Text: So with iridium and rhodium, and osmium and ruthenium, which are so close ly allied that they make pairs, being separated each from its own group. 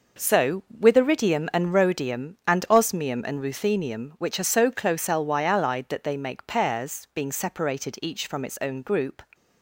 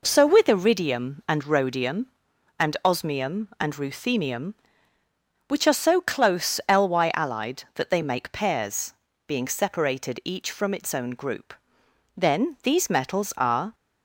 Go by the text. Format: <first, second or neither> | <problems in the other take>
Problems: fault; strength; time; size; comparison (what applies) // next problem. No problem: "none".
first | goes on to say "Then these metals are"; from 12.1 s on; 1.5 s long